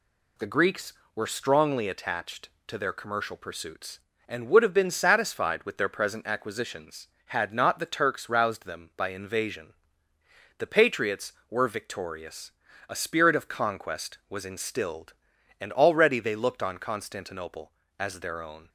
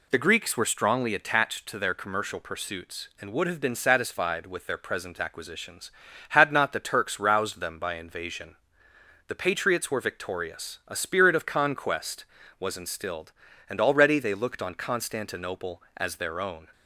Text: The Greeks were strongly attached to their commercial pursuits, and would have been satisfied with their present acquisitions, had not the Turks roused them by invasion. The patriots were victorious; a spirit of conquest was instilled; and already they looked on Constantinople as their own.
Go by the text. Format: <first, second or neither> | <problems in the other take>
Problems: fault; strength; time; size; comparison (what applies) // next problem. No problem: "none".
neither | none